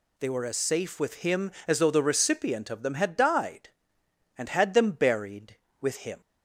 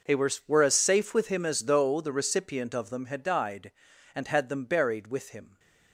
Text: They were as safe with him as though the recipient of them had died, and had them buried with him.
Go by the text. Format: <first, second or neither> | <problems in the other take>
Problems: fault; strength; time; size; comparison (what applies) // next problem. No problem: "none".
first | says "were" twice; at 0.4 s